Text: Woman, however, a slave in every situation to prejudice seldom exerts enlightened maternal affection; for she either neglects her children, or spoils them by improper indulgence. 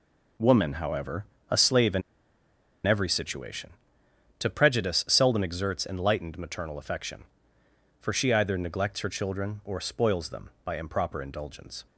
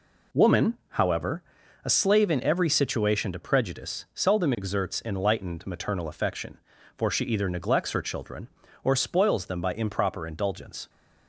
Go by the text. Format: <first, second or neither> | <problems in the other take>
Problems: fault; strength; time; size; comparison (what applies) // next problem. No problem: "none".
second | pauses between "in" and "every"; noticeable; at 2.0 s; 0.84 s long